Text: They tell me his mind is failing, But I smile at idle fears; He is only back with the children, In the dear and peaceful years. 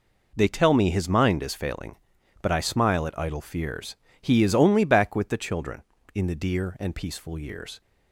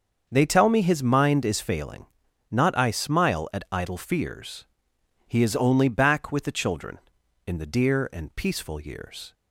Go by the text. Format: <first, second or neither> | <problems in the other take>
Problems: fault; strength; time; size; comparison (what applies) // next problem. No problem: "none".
first | starts louder than the rest; until 1.3 s; 6.5 dB // says "Not" for "But"; at 2.5 s